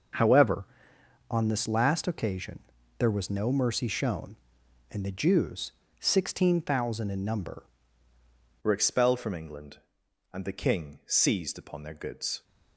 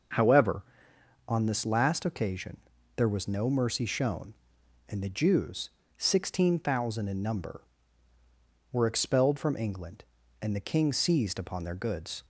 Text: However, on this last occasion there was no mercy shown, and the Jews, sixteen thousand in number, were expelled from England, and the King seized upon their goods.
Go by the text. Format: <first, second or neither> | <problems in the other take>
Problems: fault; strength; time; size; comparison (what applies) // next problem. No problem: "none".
second | pauses between "occasion" and "there"; at 2.5 s; 0.40 s long; also in the second // changes voice at "were"; from 8.6 s on; 3.8 s long